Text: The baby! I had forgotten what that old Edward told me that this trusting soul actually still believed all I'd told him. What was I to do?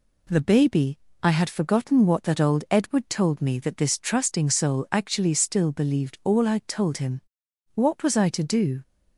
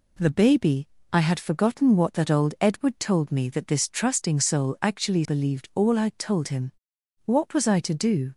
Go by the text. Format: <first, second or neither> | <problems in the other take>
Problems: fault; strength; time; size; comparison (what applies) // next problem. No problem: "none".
first | skips "still"; at 5.2 s